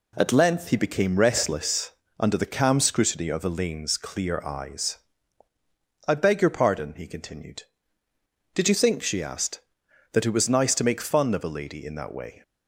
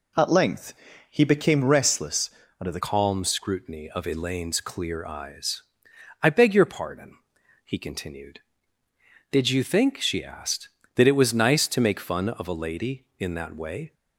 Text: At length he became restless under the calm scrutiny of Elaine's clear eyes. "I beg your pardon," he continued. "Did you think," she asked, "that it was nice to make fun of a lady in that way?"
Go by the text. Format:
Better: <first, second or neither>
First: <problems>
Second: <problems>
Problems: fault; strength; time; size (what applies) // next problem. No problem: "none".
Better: first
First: pauses between "restless" and "under"; slight; at 1.9 s; 0.28 s long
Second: pauses between "length" and "he"; slight; at 0.7 s; 0.36 s long // pauses between "restless" and "under"; slight; at 2.2 s; 0.30 s long // changes voice at "calm"; from 2.7 s on; 11.2 s long